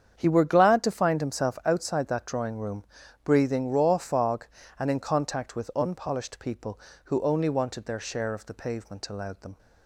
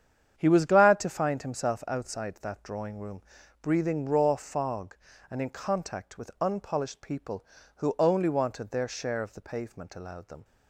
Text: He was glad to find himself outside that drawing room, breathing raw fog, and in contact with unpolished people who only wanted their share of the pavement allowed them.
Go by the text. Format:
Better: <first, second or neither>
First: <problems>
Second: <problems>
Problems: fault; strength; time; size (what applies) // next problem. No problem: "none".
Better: second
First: starts louder than the rest; strong; until 1.2 s; 8 dB // says "were" for "was"; at 0.2 s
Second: starts louder than the rest; strong; until 1.4 s; 8.5 dB